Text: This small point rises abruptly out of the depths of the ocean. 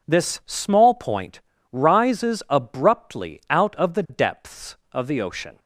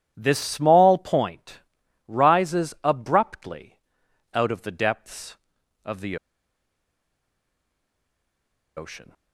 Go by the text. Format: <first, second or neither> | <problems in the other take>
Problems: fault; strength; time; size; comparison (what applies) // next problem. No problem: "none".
first | pauses between "point" and "rises"; noticeable; at 1.5 s; 0.48 s long; slight in the first // pauses between "abruptly" and "out"; noticeable; at 3.8 s; 0.52 s long // pauses between "the" and "ocean"; strong; at 6.1 s; 2.6 s long